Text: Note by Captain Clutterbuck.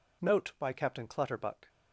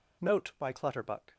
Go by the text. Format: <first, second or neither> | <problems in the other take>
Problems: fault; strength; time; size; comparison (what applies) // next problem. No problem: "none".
first | skips "Captain"; at 0.7 s